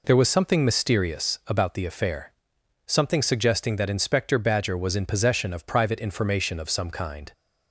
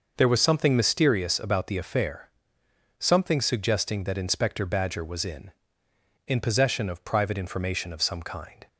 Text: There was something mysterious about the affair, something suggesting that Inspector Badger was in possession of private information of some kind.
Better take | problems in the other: first | says "in" twice; at 6.2 s

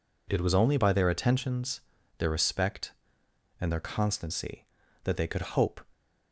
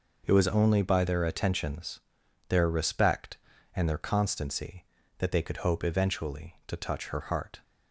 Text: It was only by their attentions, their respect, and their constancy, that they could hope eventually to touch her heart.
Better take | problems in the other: second | stops before "eventually to touch her heart"; at 5.9 s

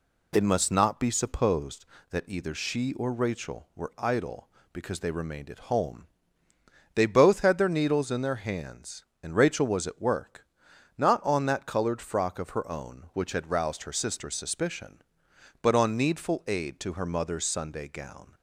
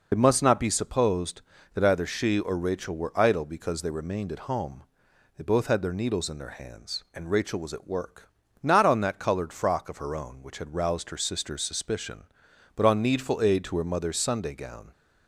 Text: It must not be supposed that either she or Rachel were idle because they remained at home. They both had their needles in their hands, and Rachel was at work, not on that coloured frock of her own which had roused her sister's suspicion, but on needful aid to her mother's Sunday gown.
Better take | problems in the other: first | loses the start of "It"; at 0.1 s; 40 ms

